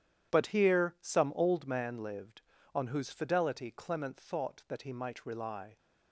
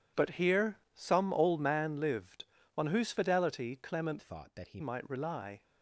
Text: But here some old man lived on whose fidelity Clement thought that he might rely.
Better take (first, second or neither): first